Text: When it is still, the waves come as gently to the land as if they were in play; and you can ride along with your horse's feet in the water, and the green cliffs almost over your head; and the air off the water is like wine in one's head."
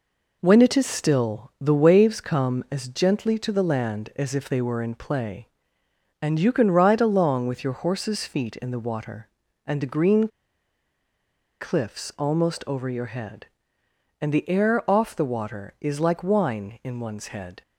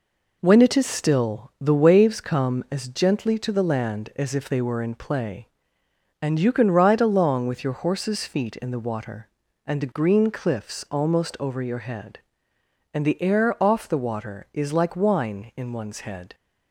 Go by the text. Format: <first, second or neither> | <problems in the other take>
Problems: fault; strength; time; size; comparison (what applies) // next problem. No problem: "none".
second | pauses between "green" and "cliffs"; strong; at 10.2 s; 1.3 s long